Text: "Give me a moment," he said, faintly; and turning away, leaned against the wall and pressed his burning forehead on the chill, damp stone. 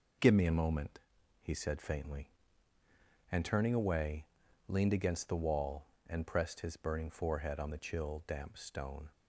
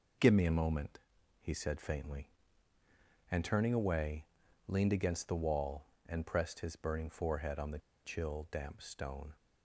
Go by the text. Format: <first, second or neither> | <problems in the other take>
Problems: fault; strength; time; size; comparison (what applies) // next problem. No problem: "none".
first | pauses between "the" and "chill"; slight; at 7.7 s; 0.25 s long